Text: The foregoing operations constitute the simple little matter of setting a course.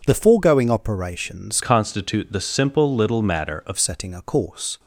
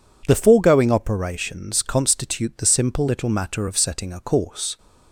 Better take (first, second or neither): second